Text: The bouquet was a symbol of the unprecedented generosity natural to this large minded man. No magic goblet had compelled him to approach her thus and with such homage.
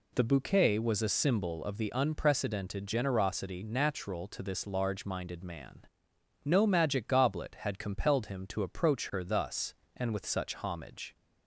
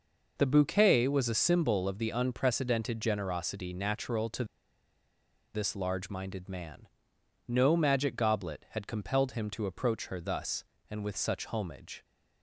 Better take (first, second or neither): first